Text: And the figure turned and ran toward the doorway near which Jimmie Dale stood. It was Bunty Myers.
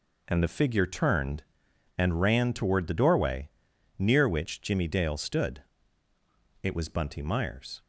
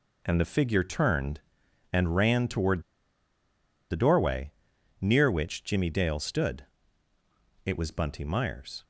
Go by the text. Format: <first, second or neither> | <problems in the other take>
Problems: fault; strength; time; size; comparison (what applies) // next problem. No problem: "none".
first | pauses between "toward" and "the"; at 2.8 s; 1.0 s long // pauses between "doorway" and "near"; noticeable; at 4.5 s; 0.50 s long; noticeable in the first